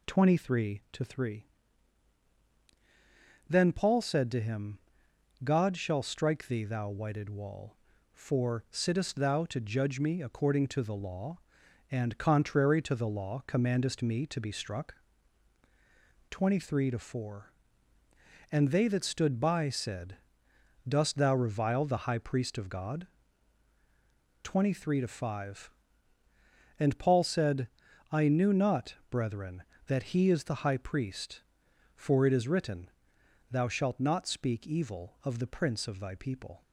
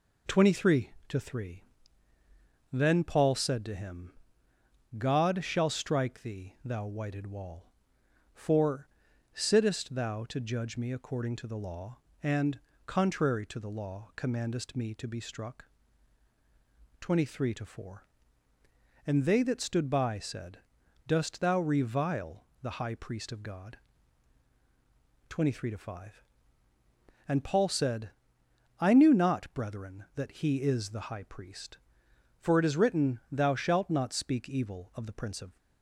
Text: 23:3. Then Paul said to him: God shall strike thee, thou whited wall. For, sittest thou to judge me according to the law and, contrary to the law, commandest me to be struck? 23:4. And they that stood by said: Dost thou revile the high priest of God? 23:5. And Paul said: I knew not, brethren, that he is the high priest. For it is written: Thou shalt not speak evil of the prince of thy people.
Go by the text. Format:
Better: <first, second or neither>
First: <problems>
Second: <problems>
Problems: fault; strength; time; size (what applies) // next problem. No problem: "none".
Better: first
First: none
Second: pauses between "revile" and "the"; slight; at 22.4 s; 0.20 s long // stops before "thy people"; at 35.5 s